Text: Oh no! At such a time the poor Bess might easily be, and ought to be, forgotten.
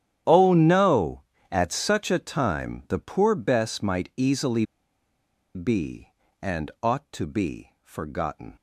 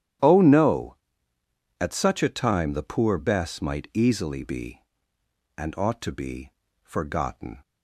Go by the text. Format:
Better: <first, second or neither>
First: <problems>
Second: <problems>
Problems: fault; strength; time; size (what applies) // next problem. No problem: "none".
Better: second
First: starts louder than the rest; strong; until 1.5 s; 10.5 dB // pauses between "easily" and "be"; noticeable; at 4.6 s; 0.89 s long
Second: starts louder than the rest; strong; until 2.0 s; 11 dB